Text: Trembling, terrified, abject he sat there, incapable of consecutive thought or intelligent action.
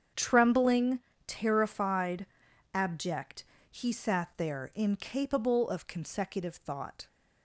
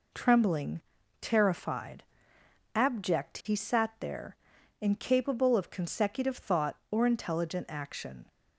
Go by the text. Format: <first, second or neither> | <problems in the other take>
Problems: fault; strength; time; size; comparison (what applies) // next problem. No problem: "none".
second | starts louder than the rest; strong; until 1.3 s; 7.5 dB // pauses between "abject" and "he"; slight; at 3.4 s; 0.26 s long // stops before "or intelligent action"; at 7.0 s